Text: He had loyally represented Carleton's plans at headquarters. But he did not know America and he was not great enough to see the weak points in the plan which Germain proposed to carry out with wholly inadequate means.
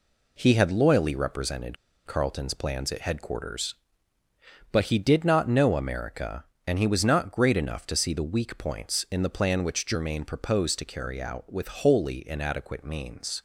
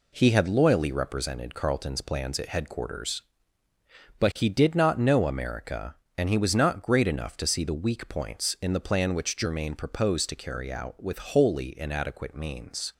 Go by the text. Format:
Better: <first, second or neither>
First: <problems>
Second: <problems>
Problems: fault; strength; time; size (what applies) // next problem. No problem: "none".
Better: second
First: pauses between "represented" and "Carleton's"; slight; at 1.7 s; 0.31 s long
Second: none